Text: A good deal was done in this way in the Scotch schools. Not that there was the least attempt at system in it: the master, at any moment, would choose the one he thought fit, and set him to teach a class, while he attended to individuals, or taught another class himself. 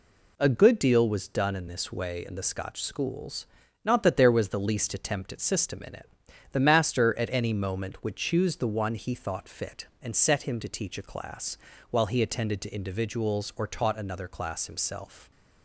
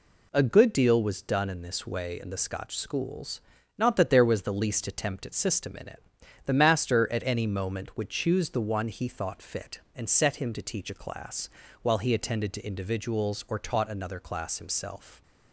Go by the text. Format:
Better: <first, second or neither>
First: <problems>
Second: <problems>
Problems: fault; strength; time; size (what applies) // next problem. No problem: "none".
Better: neither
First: none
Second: none